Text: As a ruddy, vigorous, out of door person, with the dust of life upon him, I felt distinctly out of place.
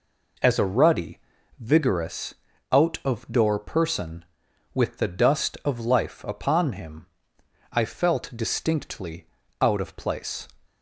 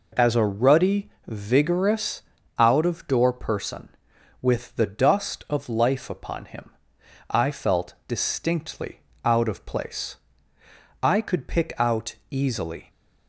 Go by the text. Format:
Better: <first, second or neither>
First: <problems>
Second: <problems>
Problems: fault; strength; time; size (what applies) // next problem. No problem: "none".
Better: first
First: pauses between "distinctly" and "out"; slight; at 9.2 s; 0.34 s long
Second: pauses between "distinctly" and "out"; slight; at 8.9 s; 0.24 s long // goes on to say "I could pick out easily"; strong; from 11.0 s on; 1.8 s long